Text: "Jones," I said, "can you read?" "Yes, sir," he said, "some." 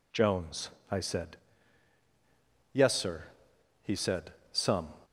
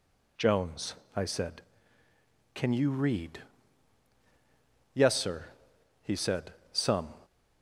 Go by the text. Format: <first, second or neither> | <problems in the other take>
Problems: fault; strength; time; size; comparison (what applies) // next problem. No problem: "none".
second | skips "can you read"; at 2.0 s